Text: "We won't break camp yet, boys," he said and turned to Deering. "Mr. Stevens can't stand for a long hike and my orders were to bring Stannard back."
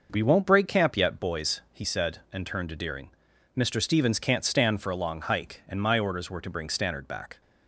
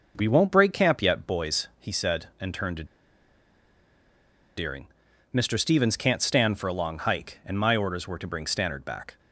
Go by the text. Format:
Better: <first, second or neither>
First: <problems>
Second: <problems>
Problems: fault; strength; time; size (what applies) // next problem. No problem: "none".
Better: first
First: none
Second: pauses between "to" and "Deering"; strong; at 2.8 s; 1.7 s long